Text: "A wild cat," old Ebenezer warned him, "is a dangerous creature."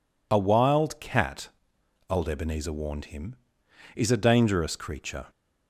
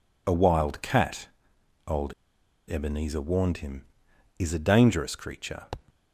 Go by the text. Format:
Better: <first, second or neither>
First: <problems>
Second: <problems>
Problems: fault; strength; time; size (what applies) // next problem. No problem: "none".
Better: first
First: none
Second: pauses between "old" and "Ebenezer"; noticeable; at 2.1 s; 0.55 s long